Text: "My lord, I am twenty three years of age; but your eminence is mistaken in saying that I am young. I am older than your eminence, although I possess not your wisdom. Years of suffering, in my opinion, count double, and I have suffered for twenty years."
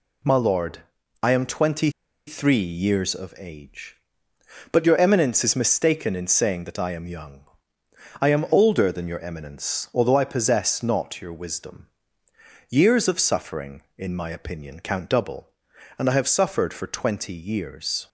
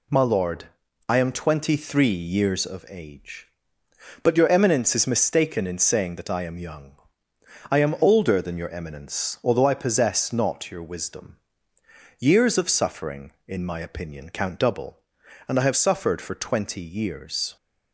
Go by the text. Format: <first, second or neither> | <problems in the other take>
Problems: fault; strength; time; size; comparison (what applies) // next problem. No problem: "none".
second | pauses between "twenty" and "three"; at 1.8 s; 0.37 s long